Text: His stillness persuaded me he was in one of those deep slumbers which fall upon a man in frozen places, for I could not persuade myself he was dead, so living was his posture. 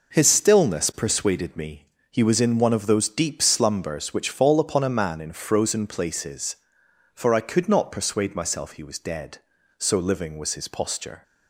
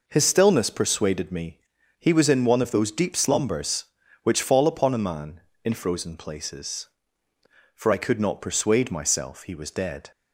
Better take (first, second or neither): first